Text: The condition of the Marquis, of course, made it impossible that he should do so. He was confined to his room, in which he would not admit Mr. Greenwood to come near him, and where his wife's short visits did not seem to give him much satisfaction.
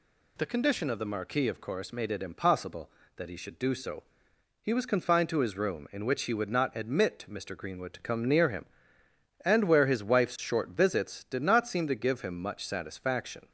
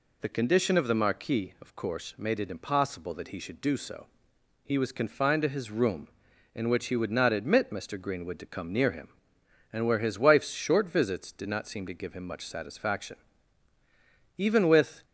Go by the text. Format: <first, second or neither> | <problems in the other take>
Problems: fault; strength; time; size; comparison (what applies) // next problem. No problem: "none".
first | goes on to say "Even with"; noticeable; from 14.3 s on; 0.68 s long